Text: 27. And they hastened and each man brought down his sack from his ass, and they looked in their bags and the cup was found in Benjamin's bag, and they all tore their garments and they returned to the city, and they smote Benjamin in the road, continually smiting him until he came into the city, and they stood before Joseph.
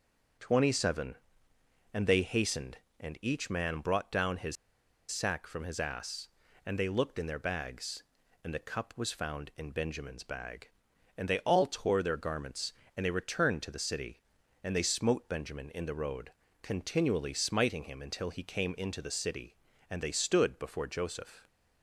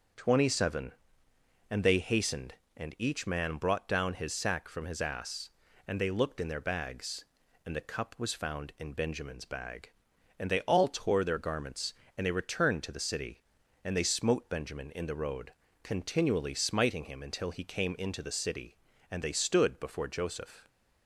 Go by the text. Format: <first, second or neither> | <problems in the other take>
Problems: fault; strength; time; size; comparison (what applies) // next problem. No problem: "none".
second | starts louder than the rest; until 2.1 s; 7 dB; also in the second // pauses between "his" and "sack"; noticeable; at 4.5 s; 0.55 s long